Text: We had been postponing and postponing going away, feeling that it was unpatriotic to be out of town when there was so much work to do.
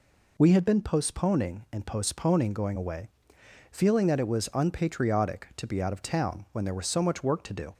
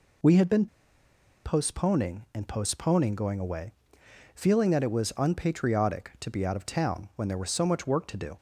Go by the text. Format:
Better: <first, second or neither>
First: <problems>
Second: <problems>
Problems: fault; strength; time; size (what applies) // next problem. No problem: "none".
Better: first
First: none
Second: pauses between "been" and "postponing"; noticeable; at 0.6 s; 0.78 s long